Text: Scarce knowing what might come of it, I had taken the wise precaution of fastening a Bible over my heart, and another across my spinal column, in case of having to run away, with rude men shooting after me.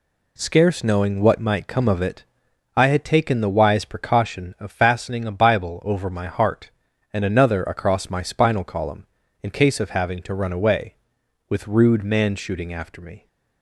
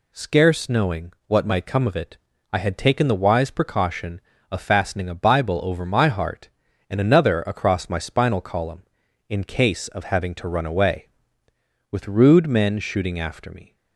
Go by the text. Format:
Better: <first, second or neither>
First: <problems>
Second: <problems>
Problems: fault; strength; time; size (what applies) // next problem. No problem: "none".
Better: second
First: says "man" for "men"; at 12.0 s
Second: none